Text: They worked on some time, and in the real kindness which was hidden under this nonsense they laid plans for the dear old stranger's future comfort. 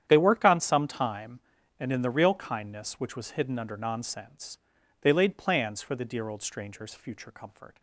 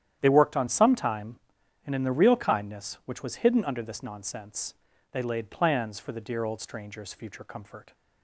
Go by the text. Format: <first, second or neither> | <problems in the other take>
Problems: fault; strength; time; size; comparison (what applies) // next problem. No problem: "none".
second | starts louder than the rest; strong; until 1.0 s; 10 dB; strong in the second // skips "this"; at 3.7 s // pauses between "nonsense" and "they"; at 4.5 s; 0.44 s long; also in the second